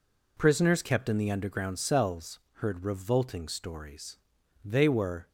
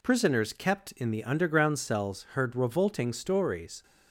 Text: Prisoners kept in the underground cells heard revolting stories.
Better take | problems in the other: second | pauses between "cells" and "heard"; slight; at 2.3 s; 0.20 s long // goes on to say "They were"; noticeable; from 4.6 s on; 0.64 s long

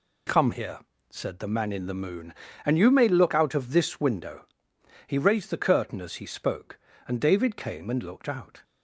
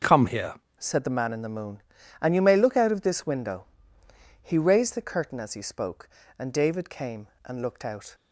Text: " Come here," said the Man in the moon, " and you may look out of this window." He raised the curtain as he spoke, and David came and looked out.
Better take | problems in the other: first | starts louder than the rest; until 1.2 s; 6.5 dB // changes voice at "said"; from 0.7 s on; 7.4 s long

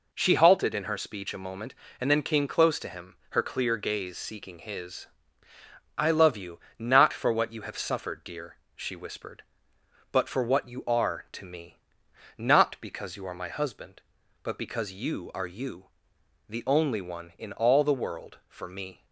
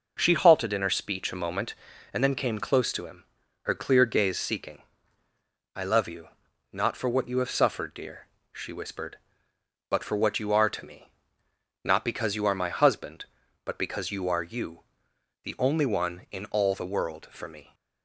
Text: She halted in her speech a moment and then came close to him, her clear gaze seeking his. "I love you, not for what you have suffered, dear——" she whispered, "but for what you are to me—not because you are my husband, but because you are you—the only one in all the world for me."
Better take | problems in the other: first | skips "his"; at 5.2 s

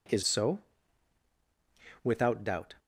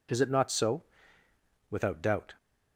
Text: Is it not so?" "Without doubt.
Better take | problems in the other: second | skips "it not"; at 0.2 s

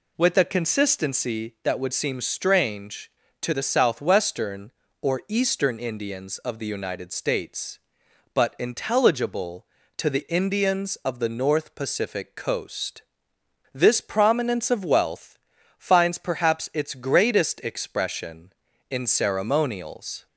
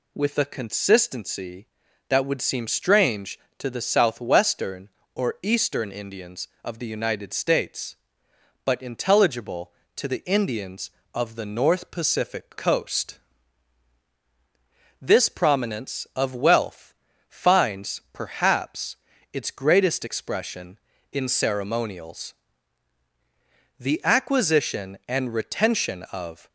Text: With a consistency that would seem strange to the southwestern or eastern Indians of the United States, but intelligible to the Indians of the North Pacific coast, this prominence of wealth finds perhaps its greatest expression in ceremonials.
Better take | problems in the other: first | pauses between "wealth" and "finds"; slight; at 16.9 s; 0.36 s long; also in the first // pauses between "perhaps" and "its"; at 18.9 s; 0.38 s long // goes on to say "The acquisition and retention of"; strong; from 23.7 s on; 2.7 s long

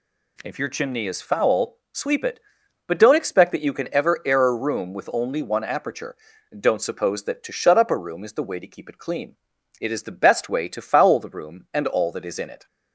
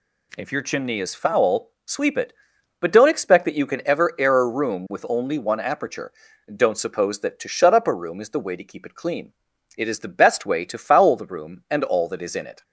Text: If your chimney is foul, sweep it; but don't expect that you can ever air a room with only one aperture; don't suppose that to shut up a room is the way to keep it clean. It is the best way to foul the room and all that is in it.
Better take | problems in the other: neither | none

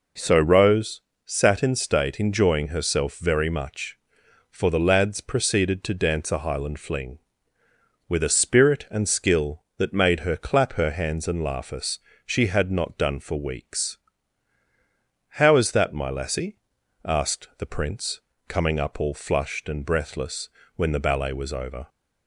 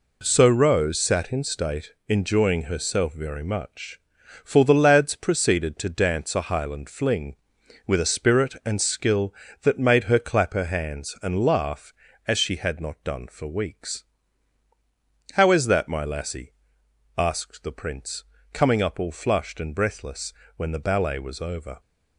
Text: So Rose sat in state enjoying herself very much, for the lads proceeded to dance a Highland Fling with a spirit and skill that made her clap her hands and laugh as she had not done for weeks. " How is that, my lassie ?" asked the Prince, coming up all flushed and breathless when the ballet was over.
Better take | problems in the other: second | pauses between "Rose" and "sat"; slight; at 1.0 s; 0.24 s long // says "us" for "as"; at 11.7 s // pauses between "breathless" and "when"; slight; at 20.4 s; 0.28 s long; slight in the second

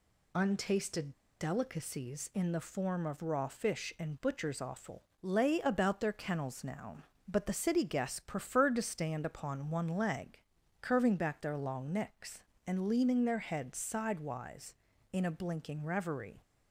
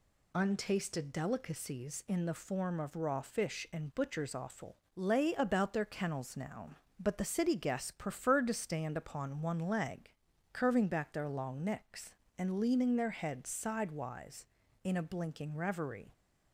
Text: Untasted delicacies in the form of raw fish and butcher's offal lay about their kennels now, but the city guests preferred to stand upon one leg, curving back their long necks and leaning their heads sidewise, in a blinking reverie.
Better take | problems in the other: second | pauses between "Untasted" and "delicacies"; slight; at 1.1 s; 0.29 s long // pauses between "offal" and "lay"; slight; at 5.0 s; 0.18 s long; slight in the second

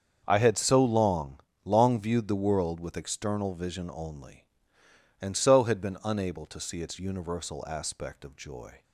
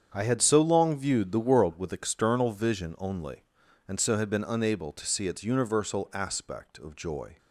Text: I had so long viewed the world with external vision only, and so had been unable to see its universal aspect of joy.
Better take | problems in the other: second | starts louder than the rest; until 1.2 s; 7 dB; strong in the second // says "long" twice; at 1.6 s

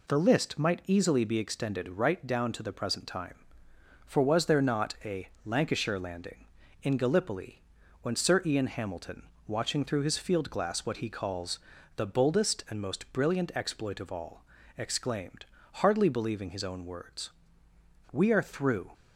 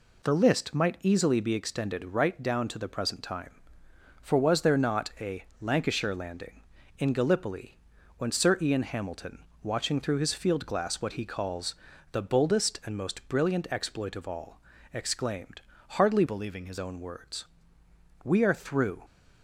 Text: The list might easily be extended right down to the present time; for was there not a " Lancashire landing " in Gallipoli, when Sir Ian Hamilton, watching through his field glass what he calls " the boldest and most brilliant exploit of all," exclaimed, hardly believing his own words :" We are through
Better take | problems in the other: first | changes voice from "believing" to "his"; from 16.2 to 16.7 s; 0.5 s long

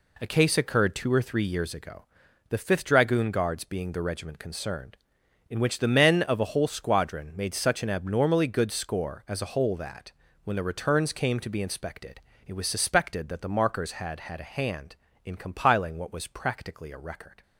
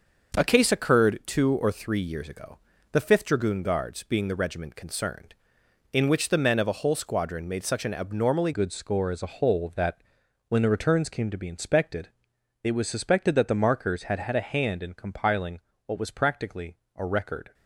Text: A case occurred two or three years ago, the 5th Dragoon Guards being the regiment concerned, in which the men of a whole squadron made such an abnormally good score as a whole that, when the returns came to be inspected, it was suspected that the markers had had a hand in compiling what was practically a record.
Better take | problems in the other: first | starts louder than the rest; until 1.4 s; 6.5 dB // changes voice at "good"; from 8.5 s on; 9.0 s long // pauses between "compiling" and "what"; slight; at 15.5 s; 0.26 s long // pauses between "practically" and "a"; slight; at 16.7 s; 0.20 s long

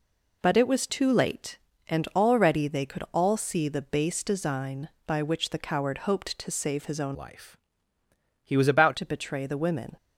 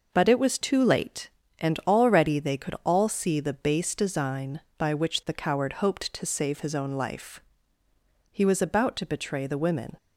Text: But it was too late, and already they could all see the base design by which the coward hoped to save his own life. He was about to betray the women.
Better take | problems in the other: second | changes voice from "life" to "about"; from 7.1 to 8.9 s; 1.8 s long

